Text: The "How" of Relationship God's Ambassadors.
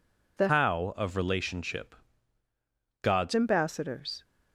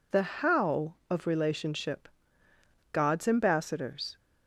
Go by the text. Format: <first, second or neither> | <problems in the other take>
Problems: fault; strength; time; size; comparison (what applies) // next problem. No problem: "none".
second | changes voice from "How" to "God's"; from 0.4 to 3.3 s; 2.9 s long // pauses between "Relationship" and "God's"; at 1.9 s; 1.0 s long; noticeable in the second